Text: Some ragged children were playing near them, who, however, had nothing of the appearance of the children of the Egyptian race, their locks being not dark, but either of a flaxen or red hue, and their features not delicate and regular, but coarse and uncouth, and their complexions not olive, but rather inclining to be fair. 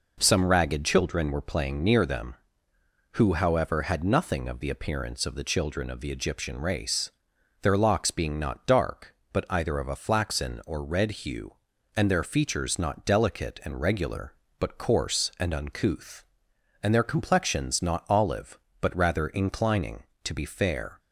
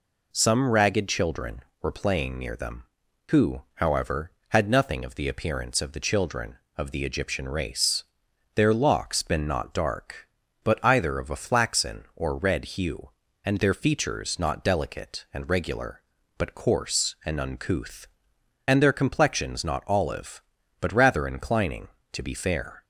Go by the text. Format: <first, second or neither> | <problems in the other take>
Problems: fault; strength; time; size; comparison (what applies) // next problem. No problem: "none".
first | says "been" for "being"; at 9.2 s